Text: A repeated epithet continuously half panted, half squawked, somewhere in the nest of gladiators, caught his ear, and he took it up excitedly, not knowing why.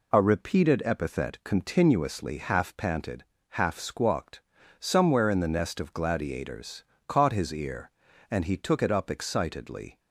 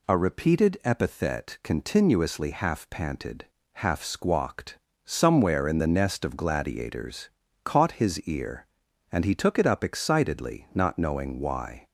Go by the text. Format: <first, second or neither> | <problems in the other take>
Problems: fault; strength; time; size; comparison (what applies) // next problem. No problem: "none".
second | stops before "not knowing why"; at 9.9 s